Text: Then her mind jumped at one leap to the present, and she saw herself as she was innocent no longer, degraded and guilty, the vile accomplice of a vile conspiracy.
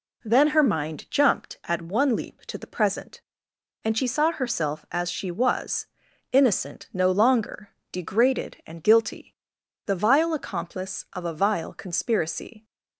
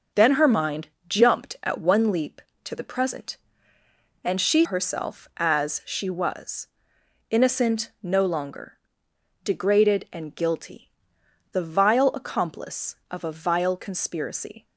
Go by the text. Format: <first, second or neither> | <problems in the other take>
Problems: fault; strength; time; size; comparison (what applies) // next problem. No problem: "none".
first | starts louder than the rest; until 1.3 s; 6 dB // pauses between "mind" and "jumped"; slight; at 0.8 s; 0.18 s long // skips "saw"; at 4.6 s // pauses between "was" and "innocent"; noticeable; at 6.6 s; 0.62 s long; also in the first